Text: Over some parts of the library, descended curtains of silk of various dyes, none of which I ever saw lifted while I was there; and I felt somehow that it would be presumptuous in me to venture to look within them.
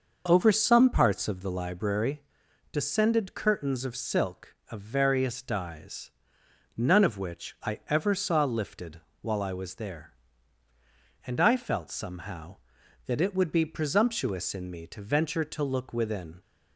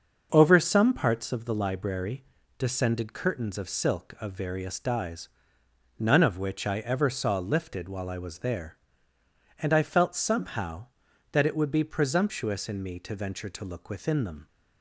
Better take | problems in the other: second | starts louder than the rest; noticeable; until 1.2 s; 6 dB; also in the second // pauses between "lifted" and "while"; slight; at 8.9 s; 0.22 s long // stops before "them"; at 16.4 s

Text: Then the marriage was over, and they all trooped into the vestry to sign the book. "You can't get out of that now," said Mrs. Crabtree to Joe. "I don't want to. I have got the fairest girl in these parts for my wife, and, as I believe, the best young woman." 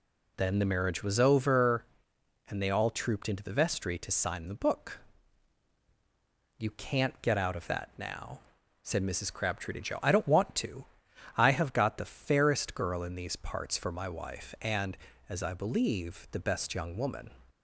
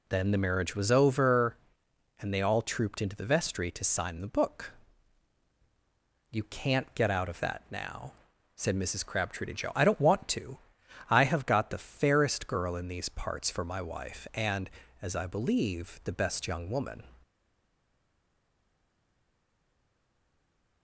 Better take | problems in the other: first | stays silent after the last word; strong; from 17.2 s on; 3.6 s long

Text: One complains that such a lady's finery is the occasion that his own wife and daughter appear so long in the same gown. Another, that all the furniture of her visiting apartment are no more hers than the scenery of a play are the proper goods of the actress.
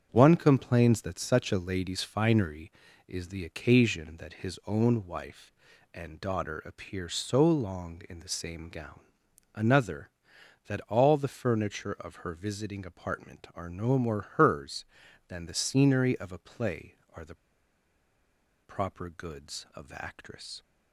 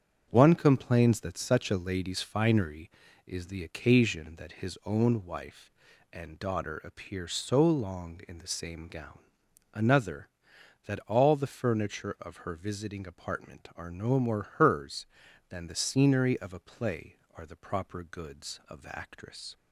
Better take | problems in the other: second | starts louder than the rest; strong; until 1.1 s; 7.5 dB; strong in the second // pauses between "more" and "hers"; slight; at 14.2 s; 0.16 s long; slight in the second // pauses between "the" and "proper"; strong; at 17.3 s; 1.2 s long

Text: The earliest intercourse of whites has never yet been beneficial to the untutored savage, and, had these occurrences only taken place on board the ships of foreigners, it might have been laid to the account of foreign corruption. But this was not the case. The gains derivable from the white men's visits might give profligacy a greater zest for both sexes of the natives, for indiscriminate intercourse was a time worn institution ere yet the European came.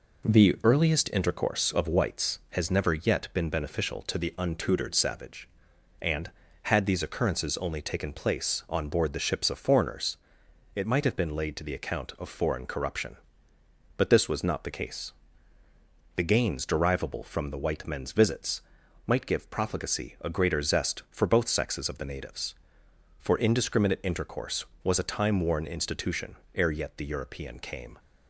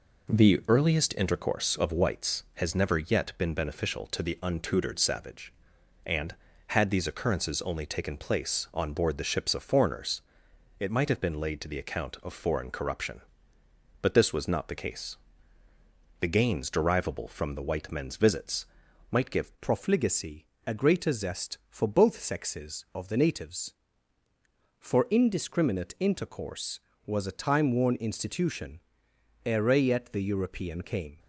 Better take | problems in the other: first | pauses between "visits" and "might"; at 18.6 s; 0.44 s long; also in the first // changes voice at "profligacy"; from 19.6 s on; 11.5 s long // pauses between "profligacy" and "a"; slight; at 20.4 s; 0.20 s long // pauses between "institution" and "ere"; noticeable; at 28.7 s; 0.66 s long; slight in the first

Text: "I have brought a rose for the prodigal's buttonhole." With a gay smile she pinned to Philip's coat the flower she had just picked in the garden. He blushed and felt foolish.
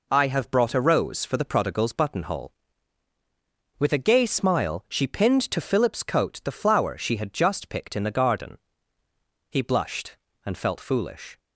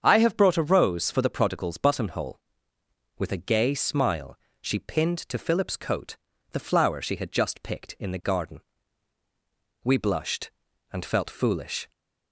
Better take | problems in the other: first | starts louder than the rest; strong; until 1.0 s; 7.5 dB // pauses between "smile" and "she"; slight; at 4.3 s; 0.22 s long // pauses between "coat" and "the"; slight; at 6.1 s; 0.36 s long // says "We" for "He"; at 9.8 s

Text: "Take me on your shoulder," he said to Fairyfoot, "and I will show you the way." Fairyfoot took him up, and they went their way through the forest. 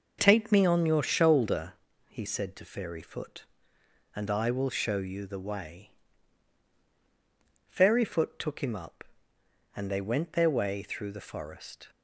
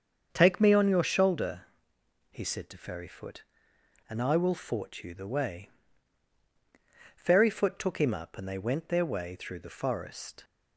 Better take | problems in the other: first | starts louder than the rest; until 1.3 s; 7 dB // says "fort" for "show"; at 4.5 s

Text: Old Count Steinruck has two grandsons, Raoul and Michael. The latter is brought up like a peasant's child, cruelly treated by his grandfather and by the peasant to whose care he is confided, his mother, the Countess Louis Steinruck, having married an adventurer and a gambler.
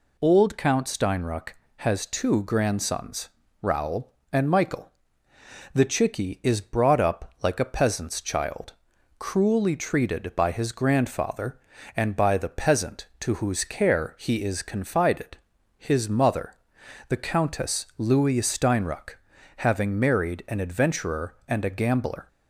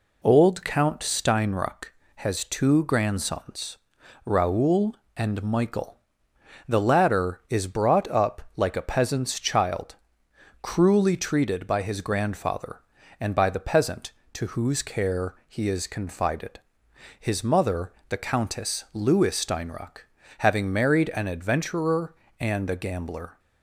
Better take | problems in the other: second | says "chicky" for "latter"; at 5.8 s

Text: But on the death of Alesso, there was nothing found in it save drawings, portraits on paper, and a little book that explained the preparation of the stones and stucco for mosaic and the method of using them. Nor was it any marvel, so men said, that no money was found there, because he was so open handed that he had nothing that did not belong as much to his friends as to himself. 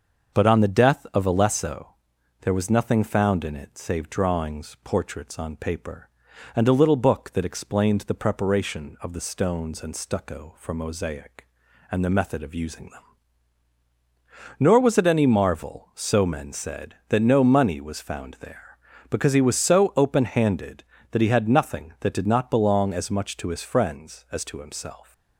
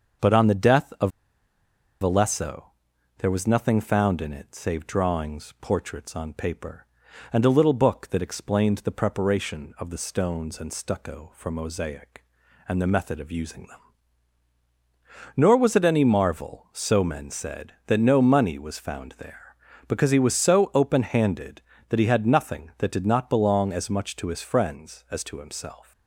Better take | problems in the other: first | starts louder than the rest; until 2.1 s; 6.5 dB; also in the first // pauses between "of" and "Alesso"; noticeable; at 1.1 s; 0.90 s long

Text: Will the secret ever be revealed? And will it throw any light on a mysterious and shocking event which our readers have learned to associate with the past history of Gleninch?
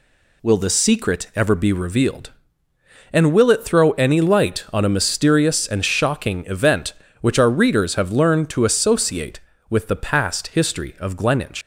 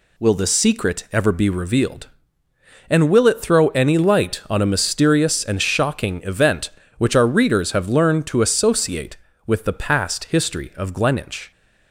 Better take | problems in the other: second | leaves "Gleninch" unfinished; at 11.6 s; 125 ms

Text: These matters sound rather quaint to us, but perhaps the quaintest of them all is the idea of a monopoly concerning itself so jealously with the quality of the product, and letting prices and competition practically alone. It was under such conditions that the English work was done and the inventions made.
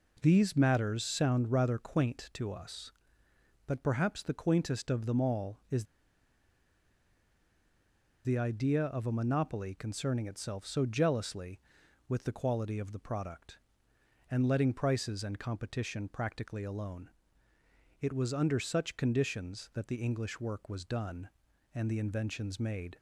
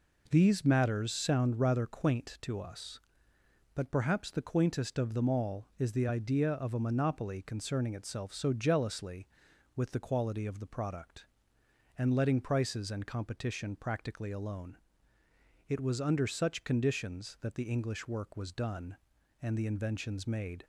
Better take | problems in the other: second | pauses between "is" and "the"; strong; at 5.8 s; 2.4 s long

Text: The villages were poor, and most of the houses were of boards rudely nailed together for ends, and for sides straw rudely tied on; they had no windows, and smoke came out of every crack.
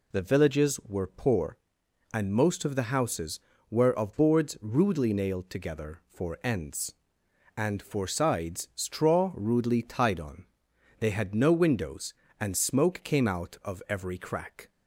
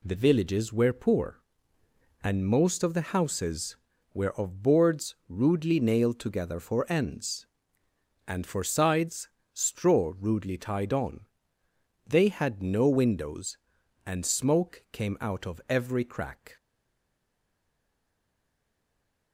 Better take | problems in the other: first | pauses between "sides" and "straw"; slight; at 9.2 s; 0.26 s long // stays silent after the last word; strong; from 16.5 s on; 2.8 s long

